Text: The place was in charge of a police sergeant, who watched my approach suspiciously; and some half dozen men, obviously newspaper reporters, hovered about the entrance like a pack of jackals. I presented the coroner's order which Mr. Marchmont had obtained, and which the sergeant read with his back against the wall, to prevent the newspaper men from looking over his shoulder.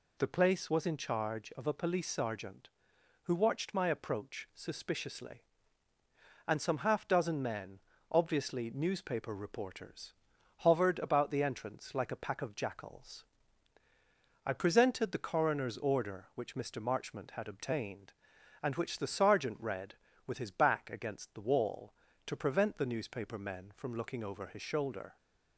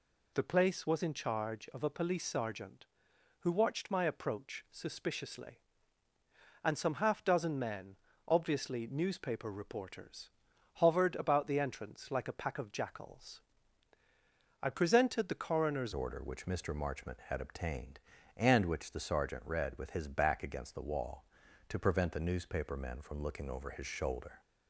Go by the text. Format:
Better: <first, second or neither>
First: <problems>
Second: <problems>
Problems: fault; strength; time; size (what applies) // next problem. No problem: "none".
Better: first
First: none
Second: changes voice at "order"; from 15.9 s on; 8.5 s long